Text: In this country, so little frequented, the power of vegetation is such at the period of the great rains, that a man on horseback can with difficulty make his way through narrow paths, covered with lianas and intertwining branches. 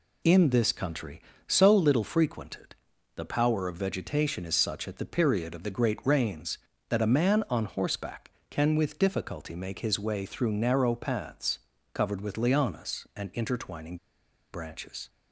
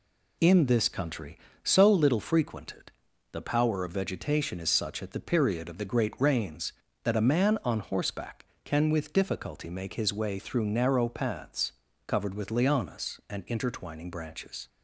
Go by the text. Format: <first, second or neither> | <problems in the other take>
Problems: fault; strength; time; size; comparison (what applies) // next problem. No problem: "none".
second | pauses between "intertwining" and "branches"; noticeable; at 13.9 s; 0.56 s long